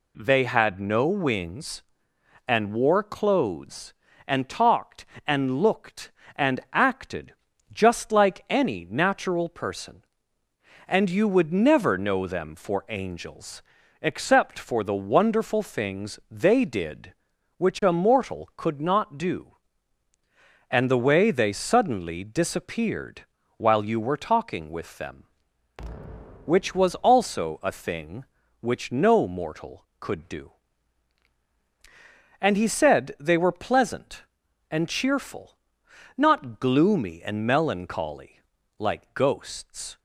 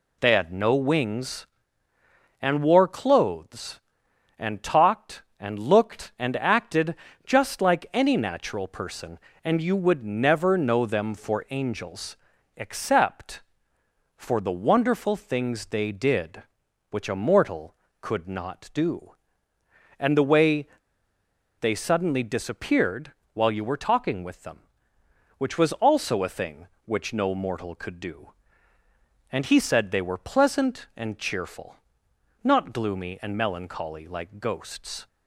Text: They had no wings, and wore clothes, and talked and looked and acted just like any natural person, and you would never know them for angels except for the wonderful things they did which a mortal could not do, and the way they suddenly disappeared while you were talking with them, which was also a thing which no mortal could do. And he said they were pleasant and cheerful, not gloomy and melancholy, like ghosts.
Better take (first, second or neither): first